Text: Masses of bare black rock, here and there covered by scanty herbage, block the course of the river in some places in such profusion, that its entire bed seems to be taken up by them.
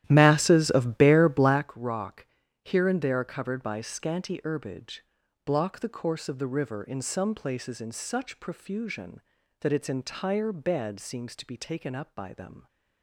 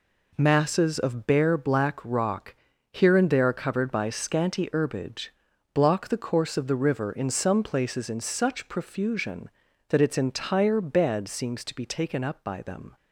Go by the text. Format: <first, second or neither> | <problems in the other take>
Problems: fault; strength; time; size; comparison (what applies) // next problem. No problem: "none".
second | starts louder than the rest; strong; until 1.7 s; 12.5 dB